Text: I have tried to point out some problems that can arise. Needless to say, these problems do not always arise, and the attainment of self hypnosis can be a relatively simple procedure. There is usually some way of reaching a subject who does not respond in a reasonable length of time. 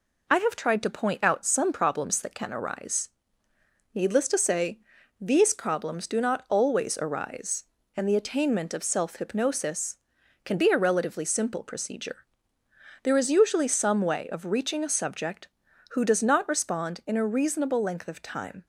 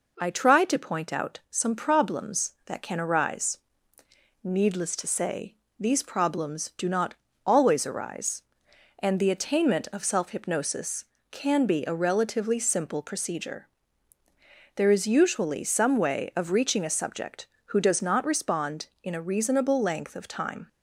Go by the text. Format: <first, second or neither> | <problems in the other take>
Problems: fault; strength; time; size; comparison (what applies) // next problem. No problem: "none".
first | skips "have"; at 0.2 s // pauses between "not" and "always"; slight; at 7.1 s; 0.32 s long